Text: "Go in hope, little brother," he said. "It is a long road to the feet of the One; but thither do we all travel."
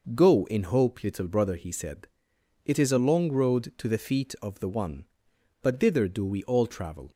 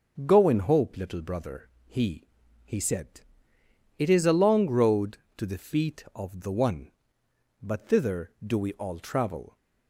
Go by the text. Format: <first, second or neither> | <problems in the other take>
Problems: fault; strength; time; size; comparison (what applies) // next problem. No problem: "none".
first | starts louder than the rest; until 1.2 s; 6.5 dB // says "he" twice; at 2.6 s